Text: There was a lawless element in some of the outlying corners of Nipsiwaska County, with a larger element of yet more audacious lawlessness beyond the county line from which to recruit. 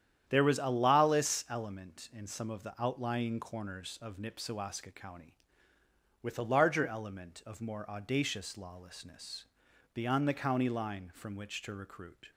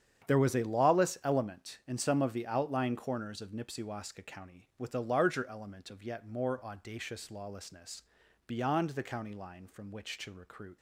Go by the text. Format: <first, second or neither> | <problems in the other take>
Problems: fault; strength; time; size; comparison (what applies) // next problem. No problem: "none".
second | starts louder than the rest; strong; until 1.2 s; 9.5 dB; strong in the second // skips "yet"; at 7.6 s // pauses between "lawlessness" and "beyond"; noticeable; at 9.4 s; 0.50 s long; also in the second